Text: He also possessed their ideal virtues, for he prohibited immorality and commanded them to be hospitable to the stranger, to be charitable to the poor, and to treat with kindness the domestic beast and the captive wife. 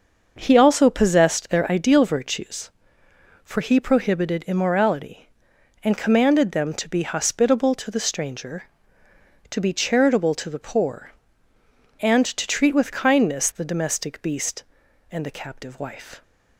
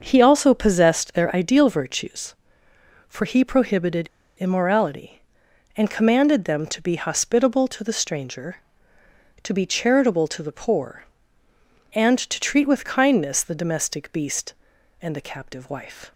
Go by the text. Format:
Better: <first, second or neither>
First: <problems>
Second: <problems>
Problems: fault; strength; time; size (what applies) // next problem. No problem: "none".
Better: first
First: starts louder than the rest; until 1.3 s; 6.5 dB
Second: starts louder than the rest; until 1.0 s; 6 dB // pauses between "prohibited" and "immorality"; slight; at 4.0 s; 0.29 s long